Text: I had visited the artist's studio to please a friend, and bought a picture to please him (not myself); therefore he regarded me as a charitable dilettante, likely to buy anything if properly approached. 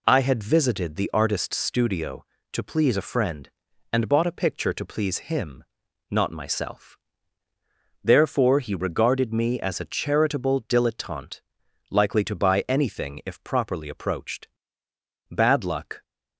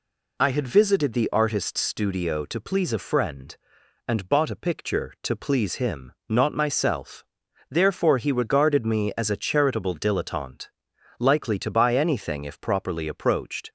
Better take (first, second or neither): second